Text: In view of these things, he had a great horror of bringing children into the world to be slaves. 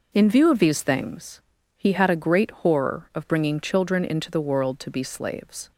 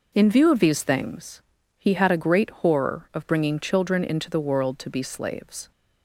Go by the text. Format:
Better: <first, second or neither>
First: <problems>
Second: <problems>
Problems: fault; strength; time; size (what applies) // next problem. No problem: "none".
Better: neither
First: none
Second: none